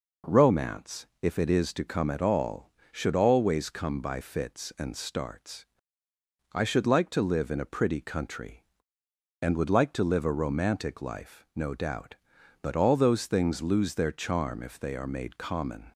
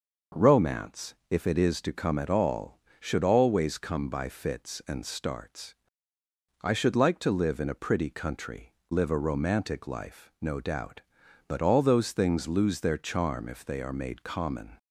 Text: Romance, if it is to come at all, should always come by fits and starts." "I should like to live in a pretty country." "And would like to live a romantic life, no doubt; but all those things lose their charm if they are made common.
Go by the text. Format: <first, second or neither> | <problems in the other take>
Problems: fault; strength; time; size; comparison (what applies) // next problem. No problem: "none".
first | skips "And would like to"; at 8.8 s